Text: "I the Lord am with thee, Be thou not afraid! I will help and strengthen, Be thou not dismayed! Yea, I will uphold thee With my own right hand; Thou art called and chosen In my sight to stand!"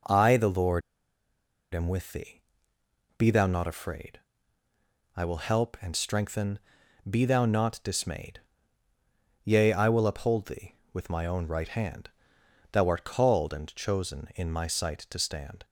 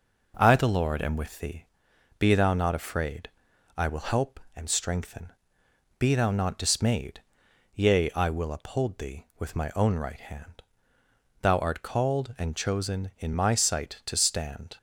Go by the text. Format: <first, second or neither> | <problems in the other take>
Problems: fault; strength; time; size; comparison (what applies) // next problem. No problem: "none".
second | pauses between "Lord" and "am"; noticeable; at 0.8 s; 0.93 s long